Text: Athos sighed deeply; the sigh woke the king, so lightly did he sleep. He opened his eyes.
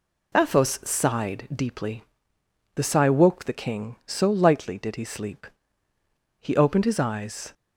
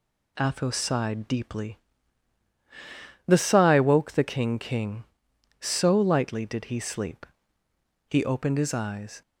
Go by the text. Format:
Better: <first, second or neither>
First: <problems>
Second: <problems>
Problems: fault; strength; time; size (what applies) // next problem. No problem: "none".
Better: first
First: none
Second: says "king" twice; at 4.5 s